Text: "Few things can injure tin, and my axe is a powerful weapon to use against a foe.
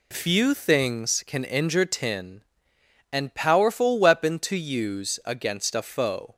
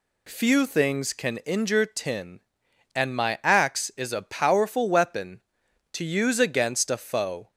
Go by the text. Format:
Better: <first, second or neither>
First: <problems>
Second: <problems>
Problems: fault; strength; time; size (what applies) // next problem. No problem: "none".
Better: second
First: skips "my axe is a"; at 3.3 s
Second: none